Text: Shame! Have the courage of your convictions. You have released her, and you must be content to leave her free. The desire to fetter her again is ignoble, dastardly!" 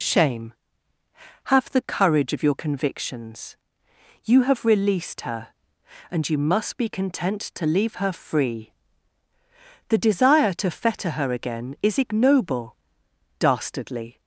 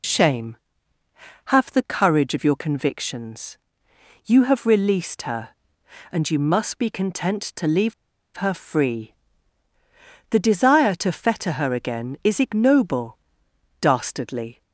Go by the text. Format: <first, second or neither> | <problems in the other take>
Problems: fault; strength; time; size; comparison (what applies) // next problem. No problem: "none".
first | pauses between "leave" and "her"; at 7.9 s; 0.43 s long